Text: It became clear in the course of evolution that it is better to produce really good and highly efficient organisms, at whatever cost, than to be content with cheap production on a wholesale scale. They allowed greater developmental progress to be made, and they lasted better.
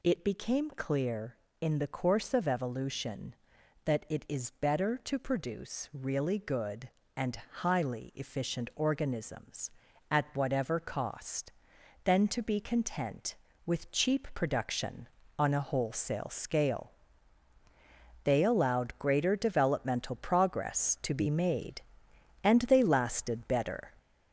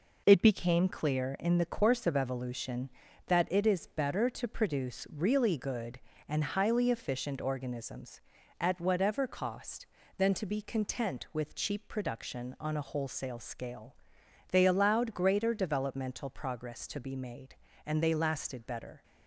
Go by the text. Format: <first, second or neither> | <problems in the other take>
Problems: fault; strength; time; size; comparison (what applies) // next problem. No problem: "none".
second | gets louder; noticeable; throughout; 4 dB // pauses between "and" and "highly"; slight; at 7.3 s; 0.20 s long